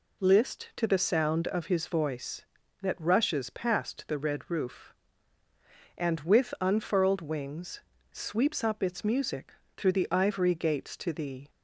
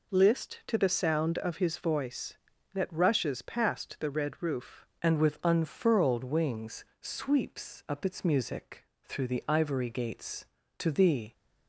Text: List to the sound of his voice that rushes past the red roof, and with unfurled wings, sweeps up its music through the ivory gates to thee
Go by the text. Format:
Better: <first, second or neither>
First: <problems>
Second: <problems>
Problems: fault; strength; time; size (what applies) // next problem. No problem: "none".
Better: first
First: pauses between "music" and "through"; slight; at 9.5 s; 0.24 s long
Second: changes voice at "and"; from 5.0 s on; 6.3 s long // pauses between "music" and "through"; slight; at 8.8 s; 0.18 s long